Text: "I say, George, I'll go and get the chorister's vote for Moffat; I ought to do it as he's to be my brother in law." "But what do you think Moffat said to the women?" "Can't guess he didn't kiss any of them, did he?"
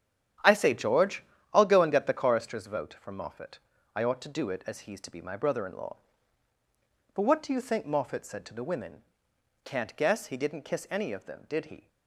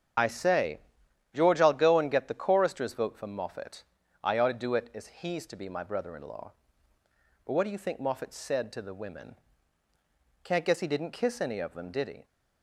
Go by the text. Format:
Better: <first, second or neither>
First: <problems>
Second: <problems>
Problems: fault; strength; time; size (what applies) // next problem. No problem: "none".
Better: first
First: starts louder than the rest; strong; until 1.7 s; 9.5 dB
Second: loses the start of "I"; at 0.1 s; 30 ms // starts louder than the rest; strong; until 1.7 s; 8.5 dB